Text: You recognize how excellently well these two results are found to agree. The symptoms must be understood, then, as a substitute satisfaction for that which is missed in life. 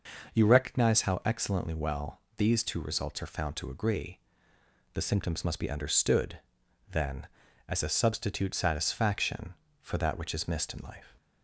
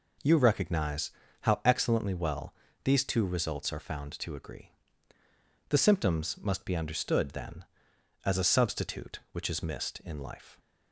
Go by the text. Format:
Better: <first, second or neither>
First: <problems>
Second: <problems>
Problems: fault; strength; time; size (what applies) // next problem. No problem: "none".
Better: first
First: pauses between "well" and "these"; slight; at 2.2 s; 0.16 s long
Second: pauses between "recognize" and "how"; slight; at 1.1 s; 0.32 s long // pauses between "well" and "these"; slight; at 2.5 s; 0.30 s long // skips "satisfaction for that"; at 9.2 s